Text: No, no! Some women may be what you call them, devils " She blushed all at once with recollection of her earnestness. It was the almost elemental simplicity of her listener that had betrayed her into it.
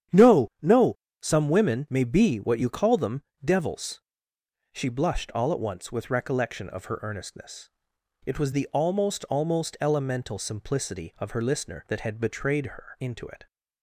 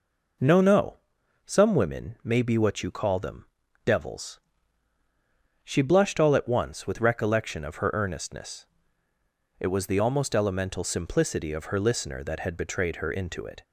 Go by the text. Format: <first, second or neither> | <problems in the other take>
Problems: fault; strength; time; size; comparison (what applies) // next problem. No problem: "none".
second | starts louder than the rest; strong; until 1.4 s; 10 dB // says "almost" twice; at 9.2 s